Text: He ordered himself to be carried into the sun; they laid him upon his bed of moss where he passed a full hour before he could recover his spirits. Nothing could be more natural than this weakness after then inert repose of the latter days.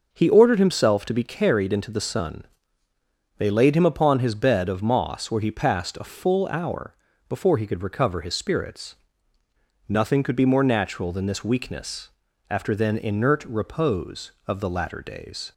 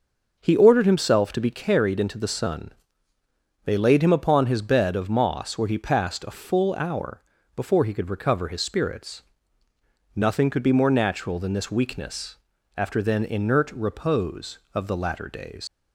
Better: first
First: pauses between "hour" and "before"; slight; at 6.9 s; 0.34 s long // pauses between "weakness" and "after"; at 12.1 s; 0.40 s long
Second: pauses between "hour" and "before"; slight; at 7.2 s; 0.34 s long // pauses between "weakness" and "after"; at 12.3 s; 0.40 s long // leaves "days" unfinished; at 15.6 s; 125 ms

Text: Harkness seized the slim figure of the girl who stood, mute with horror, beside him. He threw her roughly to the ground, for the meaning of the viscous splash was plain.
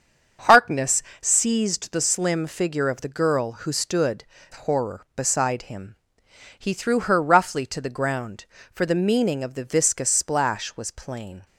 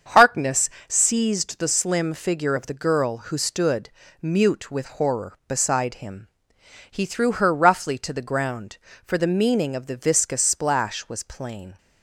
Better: second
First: starts louder than the rest; until 1.6 s; 7 dB // pauses between "Harkness" and "seized"; slight; at 1.0 s; 0.18 s long // skips "mute with"; at 4.3 s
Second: starts louder than the rest; until 1.2 s; 7 dB // pauses between "Harkness" and "seized"; slight; at 0.6 s; 0.18 s long

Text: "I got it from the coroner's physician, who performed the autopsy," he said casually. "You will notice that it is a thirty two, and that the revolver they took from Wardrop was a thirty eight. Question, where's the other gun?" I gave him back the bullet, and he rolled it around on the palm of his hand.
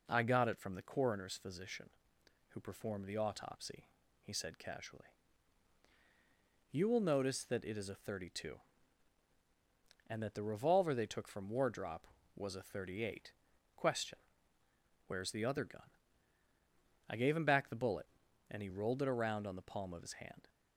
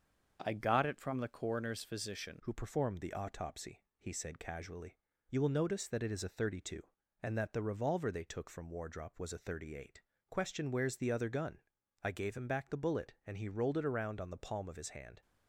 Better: first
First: none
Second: starts louder than the rest; until 1.4 s; 6.5 dB // changes voice at "who"; from 2.4 s on; 12.8 s long

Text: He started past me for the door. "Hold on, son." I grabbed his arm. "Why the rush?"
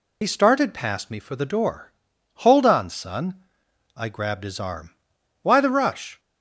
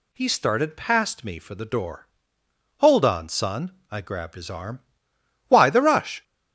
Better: second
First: loses the start of "He"; at 0.2 s; 50 ms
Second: none

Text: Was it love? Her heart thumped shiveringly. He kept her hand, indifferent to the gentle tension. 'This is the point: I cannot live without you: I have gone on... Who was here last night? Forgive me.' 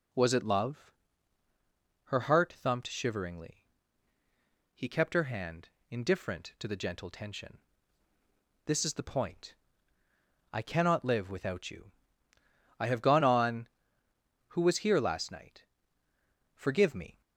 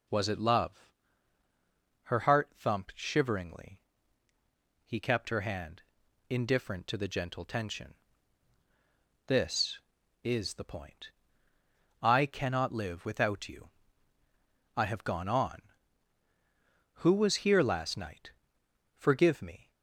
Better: neither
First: none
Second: none

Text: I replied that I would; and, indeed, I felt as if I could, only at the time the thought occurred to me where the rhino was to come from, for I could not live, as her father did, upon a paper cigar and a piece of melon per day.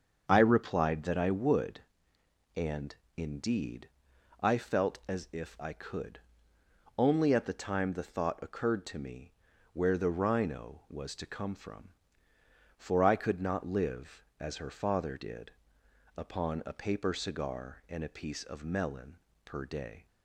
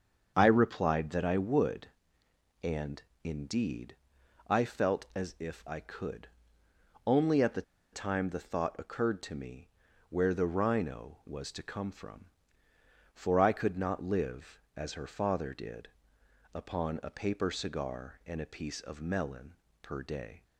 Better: first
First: starts louder than the rest; until 1.2 s; 6.5 dB // pauses between "me" and "where"; at 9.3 s; 0.40 s long // pauses between "melon" and "per"; slight; at 19.1 s; 0.26 s long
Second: starts louder than the rest; until 1.3 s; 6.5 dB // pauses between "the" and "time"; slight; at 7.6 s; 0.31 s long // pauses between "me" and "where"; at 9.6 s; 0.40 s long // pauses between "melon" and "per"; slight; at 19.5 s; 0.26 s long

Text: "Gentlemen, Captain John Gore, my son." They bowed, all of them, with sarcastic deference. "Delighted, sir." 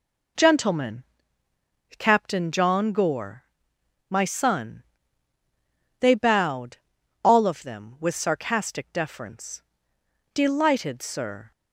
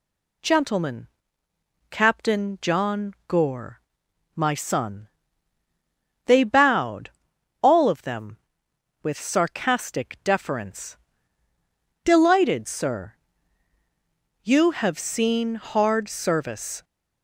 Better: first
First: none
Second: goes on to say "You have seen hard service"; strong; from 14.4 s on; 2.4 s long

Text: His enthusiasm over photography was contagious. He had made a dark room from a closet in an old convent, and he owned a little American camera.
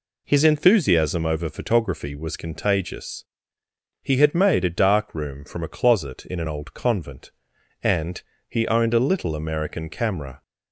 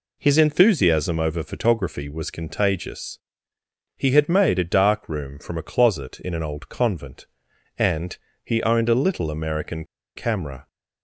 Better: first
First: pauses between "and" and "he"; slight; at 8.2 s; 0.26 s long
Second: pauses between "and" and "he"; slight; at 8.1 s; 0.26 s long // pauses between "American" and "camera"; slight; at 9.8 s; 0.30 s long

